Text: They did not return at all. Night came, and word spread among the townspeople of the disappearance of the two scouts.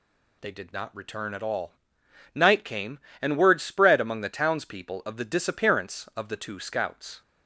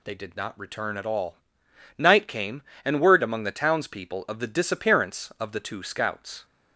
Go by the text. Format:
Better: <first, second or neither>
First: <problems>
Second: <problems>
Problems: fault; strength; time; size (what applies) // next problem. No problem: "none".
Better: first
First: none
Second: skips "spread"; at 3.2 s